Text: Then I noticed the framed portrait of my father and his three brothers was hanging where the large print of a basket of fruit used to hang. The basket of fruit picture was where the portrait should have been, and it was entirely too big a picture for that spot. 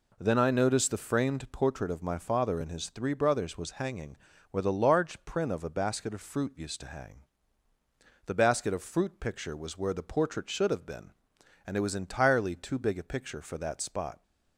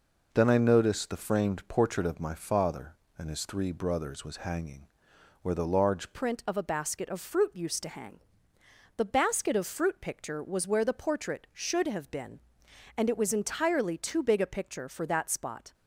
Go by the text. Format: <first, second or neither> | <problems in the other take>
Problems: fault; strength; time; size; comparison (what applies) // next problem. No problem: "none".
first | pauses between "hanging" and "where"; noticeable; at 4.8 s; 0.56 s long; slight in the first // changes voice at "print"; from 6.1 s on; 9.6 s long